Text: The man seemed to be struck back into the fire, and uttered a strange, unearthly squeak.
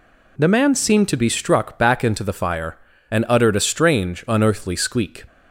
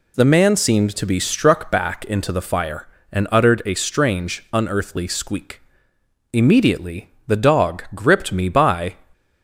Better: first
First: none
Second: goes on to say "Immediately the dog gripped me by"; strong; from 6.3 s on; 2.6 s long

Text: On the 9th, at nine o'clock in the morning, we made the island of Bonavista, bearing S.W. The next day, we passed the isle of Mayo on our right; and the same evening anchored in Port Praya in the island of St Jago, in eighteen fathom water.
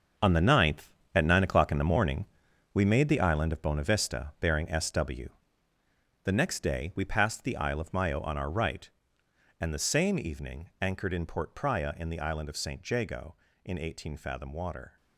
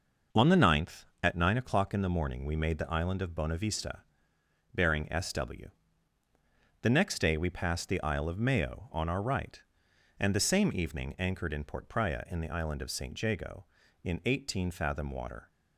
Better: second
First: gets quieter; strong; throughout; 11 dB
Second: none

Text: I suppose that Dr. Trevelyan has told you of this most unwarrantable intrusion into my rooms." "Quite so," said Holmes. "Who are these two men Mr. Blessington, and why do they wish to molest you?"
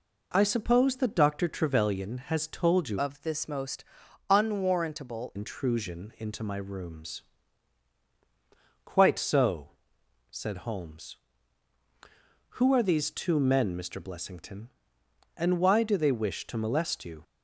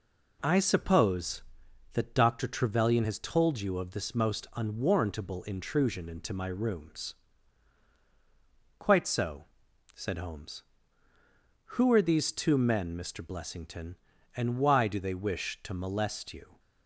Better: second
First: changes voice from "of" to "unwarrantable"; from 2.9 to 5.3 s; 2.4 s long // pauses between "most" and "unwarrantable"; noticeable; at 3.8 s; 0.46 s long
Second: none

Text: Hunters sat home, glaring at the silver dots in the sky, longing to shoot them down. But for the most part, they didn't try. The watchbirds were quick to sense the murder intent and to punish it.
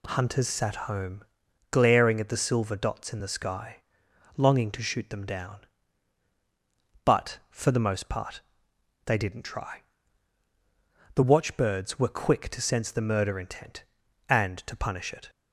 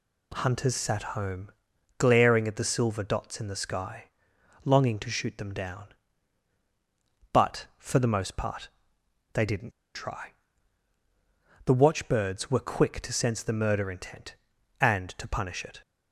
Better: first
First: none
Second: pauses between "didn't" and "try"; slight; at 9.7 s; 0.23 s long

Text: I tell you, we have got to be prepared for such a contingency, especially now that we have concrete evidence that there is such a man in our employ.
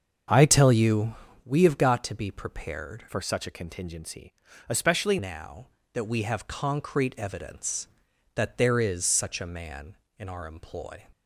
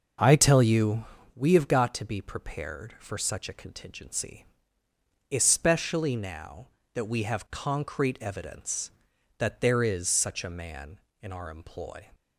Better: second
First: starts louder than the rest; until 1.5 s; 6.5 dB // changes voice from "for" to "especially"; from 3.0 to 5.1 s; 2.1 s long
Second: none

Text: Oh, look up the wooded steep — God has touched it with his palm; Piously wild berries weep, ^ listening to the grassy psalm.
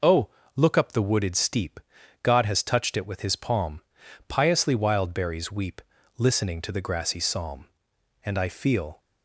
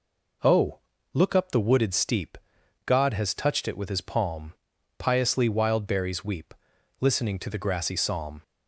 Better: second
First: goes on to say "And I feel"; noticeable; from 8.2 s on; 0.76 s long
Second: none

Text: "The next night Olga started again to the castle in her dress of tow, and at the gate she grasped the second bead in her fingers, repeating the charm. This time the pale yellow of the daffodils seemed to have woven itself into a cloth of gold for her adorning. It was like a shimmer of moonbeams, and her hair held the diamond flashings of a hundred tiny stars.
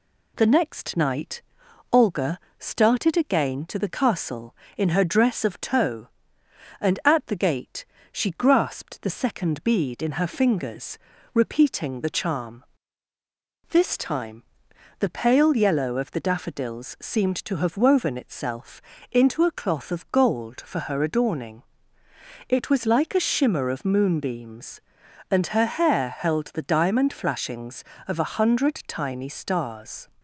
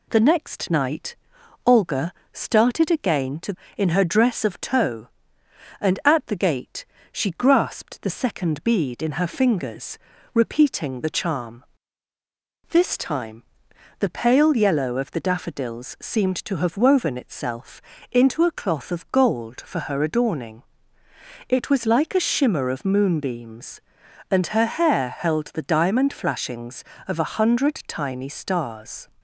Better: first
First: pauses between "night" and "Olga"; noticeable; at 1.4 s; 0.50 s long // pauses between "Olga" and "started"; slight; at 2.3 s; 0.18 s long // pauses between "gate" and "she"; slight; at 7.8 s; 0.26 s long // pauses between "time" and "the"; noticeable; at 14.4 s; 0.58 s long // pauses between "itself" and "into"; slight; at 18.8 s; 0.30 s long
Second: pauses between "night" and "Olga"; noticeable; at 1.1 s; 0.50 s long // pauses between "Olga" and "started"; slight; at 2.1 s; 0.18 s long // skips "the castle"; at 3.6 s // pauses between "gate" and "she"; slight; at 6.8 s; 0.26 s long // pauses between "time" and "the"; noticeable; at 13.4 s; 0.58 s long // pauses between "itself" and "into"; slight; at 17.8 s; 0.30 s long

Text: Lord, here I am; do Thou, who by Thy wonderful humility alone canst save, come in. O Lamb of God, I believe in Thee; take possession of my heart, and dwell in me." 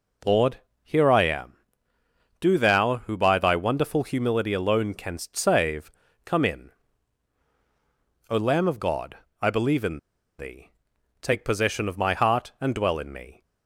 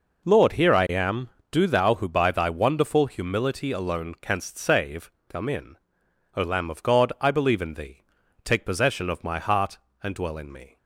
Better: second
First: pauses between "in" and "Thee"; at 9.9 s; 0.39 s long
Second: none

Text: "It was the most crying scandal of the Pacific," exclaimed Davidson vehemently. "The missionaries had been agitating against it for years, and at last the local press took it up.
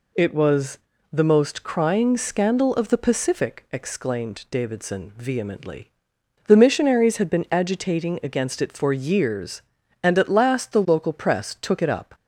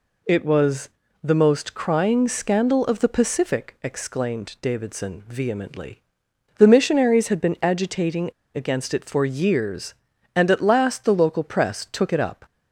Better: first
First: pauses between "was" and "the"; slight; at 0.7 s; 0.34 s long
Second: pauses between "was" and "the"; slight; at 0.8 s; 0.34 s long // pauses between "agitating" and "against"; slight; at 8.2 s; 0.25 s long

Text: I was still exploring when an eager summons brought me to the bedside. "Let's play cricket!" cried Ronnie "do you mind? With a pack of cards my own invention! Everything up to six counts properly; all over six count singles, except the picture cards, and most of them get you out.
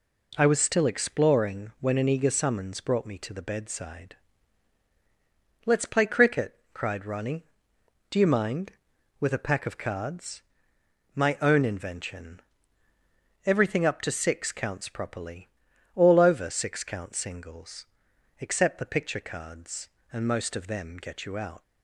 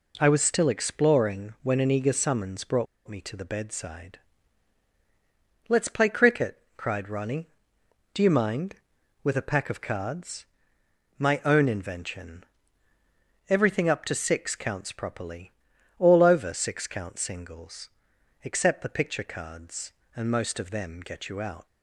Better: first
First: pauses between "cards" and "my"; noticeable; at 10.3 s; 0.74 s long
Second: pauses between "brought" and "me"; slight; at 2.8 s; 0.21 s long // pauses between "cards" and "my"; noticeable; at 10.4 s; 0.74 s long

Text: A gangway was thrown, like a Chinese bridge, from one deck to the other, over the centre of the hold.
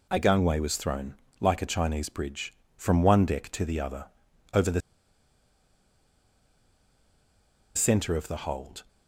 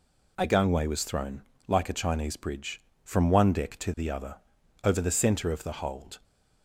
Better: second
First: pauses between "the" and "centre"; strong; at 4.7 s; 2.9 s long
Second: none

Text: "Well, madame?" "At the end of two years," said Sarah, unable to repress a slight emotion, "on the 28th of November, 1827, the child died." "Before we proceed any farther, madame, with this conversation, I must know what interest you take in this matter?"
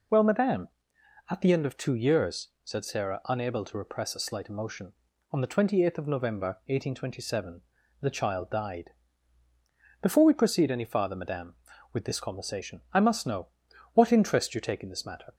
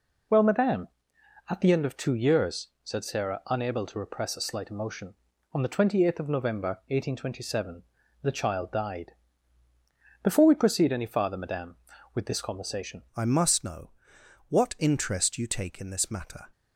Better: first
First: pauses between "know" and "what"; noticeable; at 13.4 s; 0.46 s long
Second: changes voice at "I"; from 13.1 s on; 3.4 s long // pauses between "know" and "what"; noticeable; at 13.9 s; 0.58 s long

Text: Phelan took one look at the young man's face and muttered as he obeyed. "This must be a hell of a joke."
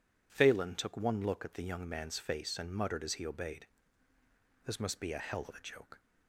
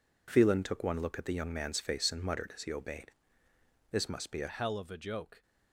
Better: first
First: none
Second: changes voice at "hell"; from 4.4 s on; 1.0 s long

